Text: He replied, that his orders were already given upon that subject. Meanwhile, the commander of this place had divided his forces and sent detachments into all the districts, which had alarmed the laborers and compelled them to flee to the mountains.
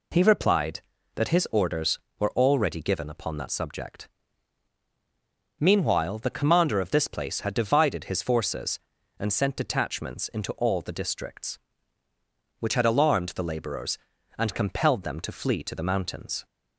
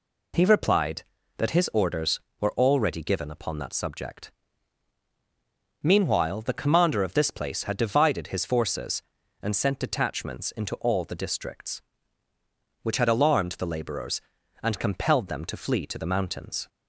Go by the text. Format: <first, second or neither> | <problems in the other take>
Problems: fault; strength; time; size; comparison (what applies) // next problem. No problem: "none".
neither | none